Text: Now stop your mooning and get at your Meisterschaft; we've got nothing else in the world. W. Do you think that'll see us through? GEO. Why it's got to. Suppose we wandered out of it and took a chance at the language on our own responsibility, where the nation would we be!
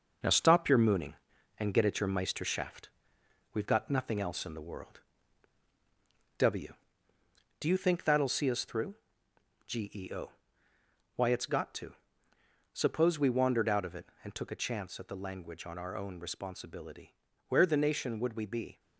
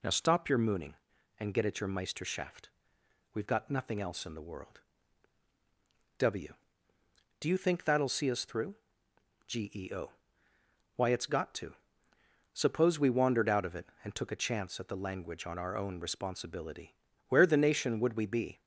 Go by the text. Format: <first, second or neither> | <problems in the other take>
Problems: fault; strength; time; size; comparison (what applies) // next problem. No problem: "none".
second | gets quieter; noticeable; throughout; 6 dB